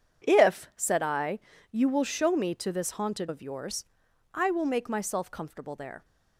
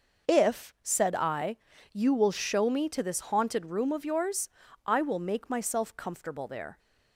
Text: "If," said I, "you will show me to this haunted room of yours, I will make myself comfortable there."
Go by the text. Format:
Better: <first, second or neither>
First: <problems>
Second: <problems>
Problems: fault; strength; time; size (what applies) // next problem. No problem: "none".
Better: second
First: skips "room"; at 3.2 s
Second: none